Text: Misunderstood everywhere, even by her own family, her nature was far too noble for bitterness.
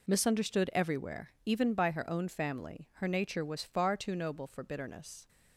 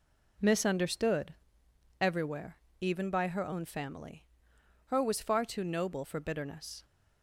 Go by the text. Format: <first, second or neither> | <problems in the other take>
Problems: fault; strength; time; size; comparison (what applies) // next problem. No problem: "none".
first | pauses between "Misunderstood" and "everywhere"; noticeable; at 1.3 s; 0.66 s long // skips "nature"; at 5.0 s